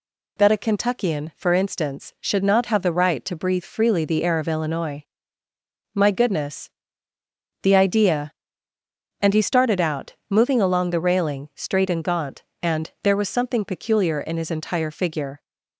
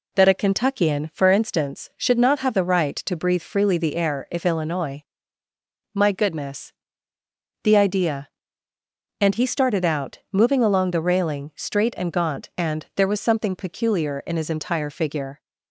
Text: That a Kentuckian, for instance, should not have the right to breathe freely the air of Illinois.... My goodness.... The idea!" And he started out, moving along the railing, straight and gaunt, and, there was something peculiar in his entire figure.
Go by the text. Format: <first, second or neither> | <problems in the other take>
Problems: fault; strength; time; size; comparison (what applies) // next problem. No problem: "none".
first | says "if" for "of"; at 4.3 s